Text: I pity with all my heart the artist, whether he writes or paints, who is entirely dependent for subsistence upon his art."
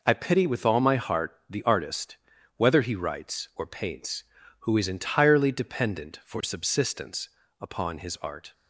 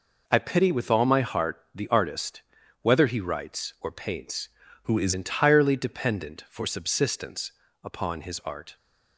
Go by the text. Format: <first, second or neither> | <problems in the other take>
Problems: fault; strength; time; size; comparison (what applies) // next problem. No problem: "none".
first | changes voice from "who" to "is"; from 4.8 to 5.1 s; 0.3 s long // pauses between "subsistence" and "upon"; slight; at 7.5 s; 0.32 s long; slight in the first